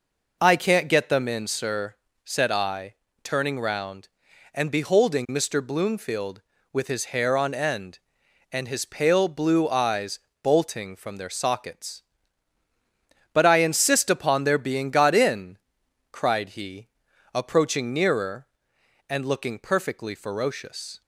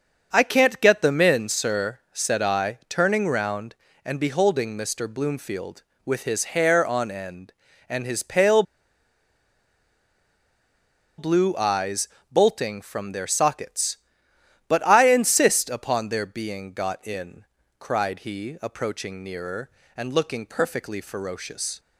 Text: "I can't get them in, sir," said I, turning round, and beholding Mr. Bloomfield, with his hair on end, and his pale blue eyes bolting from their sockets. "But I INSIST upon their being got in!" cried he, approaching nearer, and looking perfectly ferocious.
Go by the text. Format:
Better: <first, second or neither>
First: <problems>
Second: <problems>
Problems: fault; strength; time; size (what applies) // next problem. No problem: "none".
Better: first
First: pauses between "eyes" and "bolting"; slight; at 10.1 s; 0.24 s long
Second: starts louder than the rest; until 1.3 s; 6.5 dB // pauses between "pale" and "blue"; strong; at 8.6 s; 2.5 s long // pauses between "eyes" and "bolting"; slight; at 12.0 s; 0.20 s long